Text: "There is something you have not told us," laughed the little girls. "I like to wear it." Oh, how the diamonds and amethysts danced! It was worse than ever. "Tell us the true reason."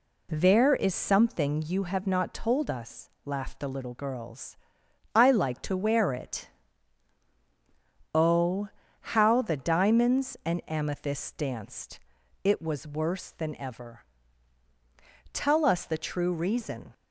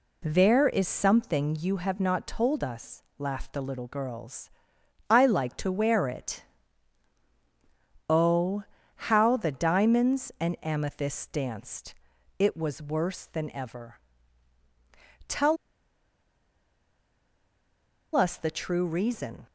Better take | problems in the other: first | pauses between "Tell" and "us"; strong; at 15.5 s; 2.5 s long

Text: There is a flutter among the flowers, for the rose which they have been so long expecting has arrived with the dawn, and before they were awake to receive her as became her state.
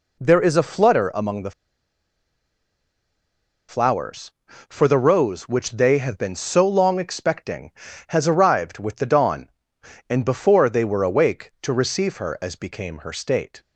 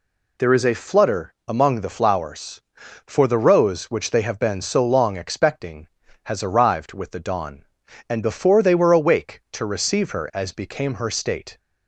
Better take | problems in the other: second | pauses between "the" and "flowers"; strong; at 1.5 s; 2.1 s long

